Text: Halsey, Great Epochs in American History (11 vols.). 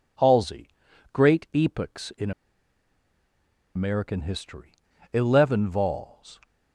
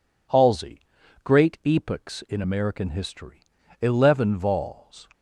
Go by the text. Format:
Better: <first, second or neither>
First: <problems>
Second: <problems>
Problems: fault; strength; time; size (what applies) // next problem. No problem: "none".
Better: second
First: pauses between "in" and "American"; strong; at 2.3 s; 1.4 s long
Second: none